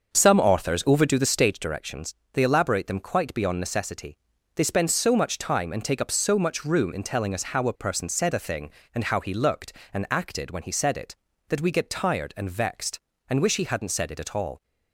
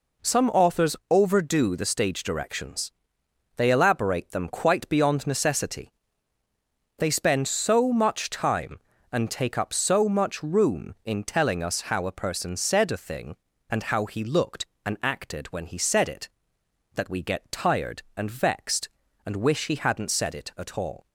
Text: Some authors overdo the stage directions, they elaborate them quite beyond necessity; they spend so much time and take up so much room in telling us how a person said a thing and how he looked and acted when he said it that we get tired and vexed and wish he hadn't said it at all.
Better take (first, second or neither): second